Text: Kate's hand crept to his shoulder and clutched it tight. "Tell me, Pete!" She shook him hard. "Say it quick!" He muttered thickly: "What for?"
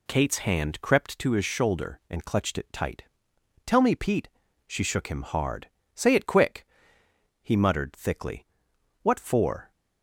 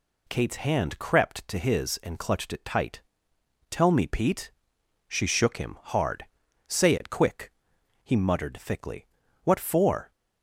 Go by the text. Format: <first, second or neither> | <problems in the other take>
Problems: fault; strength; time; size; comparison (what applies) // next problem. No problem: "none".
first | skips "shoulder"; at 2.0 s